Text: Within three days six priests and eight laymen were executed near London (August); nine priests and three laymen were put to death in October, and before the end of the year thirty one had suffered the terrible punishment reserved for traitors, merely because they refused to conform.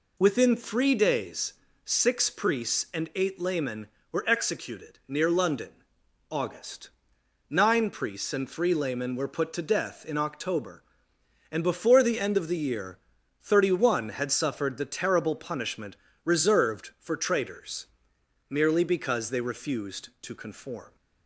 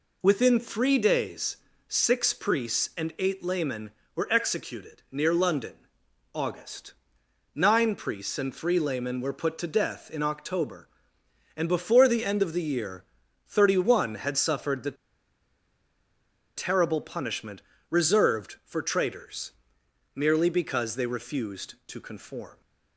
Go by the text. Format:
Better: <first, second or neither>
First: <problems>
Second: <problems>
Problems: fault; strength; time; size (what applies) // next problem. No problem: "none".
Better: first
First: pauses between "days" and "six"; slight; at 1.5 s; 0.32 s long // pauses between "year" and "thirty"; noticeable; at 12.9 s; 0.46 s long // pauses between "punishment" and "reserved"; slight; at 15.9 s; 0.26 s long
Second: pauses between "days" and "six"; slight; at 1.5 s; 0.32 s long // pauses between "year" and "thirty"; noticeable; at 13.0 s; 0.46 s long // pauses between "the" and "terrible"; strong; at 14.9 s; 1.6 s long // pauses between "punishment" and "reserved"; slight; at 17.6 s; 0.26 s long